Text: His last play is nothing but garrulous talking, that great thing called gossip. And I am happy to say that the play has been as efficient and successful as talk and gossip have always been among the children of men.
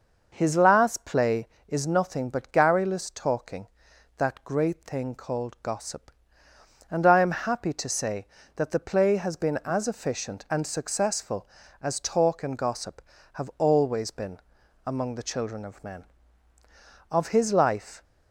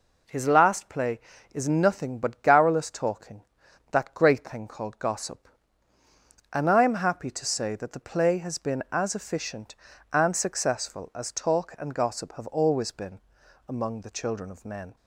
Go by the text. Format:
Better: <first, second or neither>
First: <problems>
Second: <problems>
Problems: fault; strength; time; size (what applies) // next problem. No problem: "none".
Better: second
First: pauses between "been" and "among"; noticeable; at 14.3 s; 0.48 s long // goes on to say "Of his life"; noticeable; from 17.1 s on; 0.92 s long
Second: pauses between "been" and "among"; noticeable; at 13.1 s; 0.48 s long